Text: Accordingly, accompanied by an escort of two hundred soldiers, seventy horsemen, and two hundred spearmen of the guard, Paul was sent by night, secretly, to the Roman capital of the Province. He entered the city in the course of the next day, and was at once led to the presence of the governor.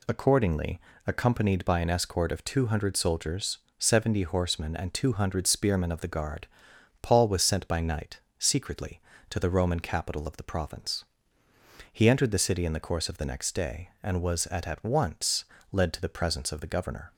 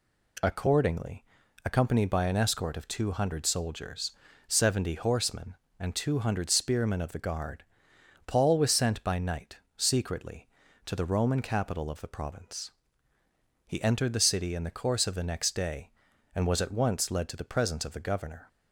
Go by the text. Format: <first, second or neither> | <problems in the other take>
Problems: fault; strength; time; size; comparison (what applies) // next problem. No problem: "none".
second | says "at" twice; at 14.6 s // pauses between "once" and "led"; slight; at 15.4 s; 0.26 s long